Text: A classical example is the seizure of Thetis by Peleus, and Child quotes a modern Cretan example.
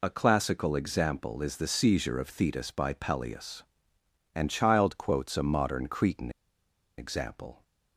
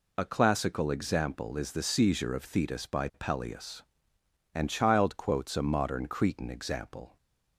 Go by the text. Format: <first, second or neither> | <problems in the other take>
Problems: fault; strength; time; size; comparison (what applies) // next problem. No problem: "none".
second | pauses between "Cretan" and "example"; noticeable; at 6.3 s; 0.67 s long